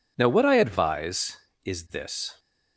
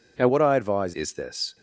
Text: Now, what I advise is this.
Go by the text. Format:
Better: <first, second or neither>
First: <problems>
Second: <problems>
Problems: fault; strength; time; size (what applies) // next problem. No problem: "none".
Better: first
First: none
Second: changes voice from "what" to "advise"; from 0.2 to 0.9 s; 0.7 s long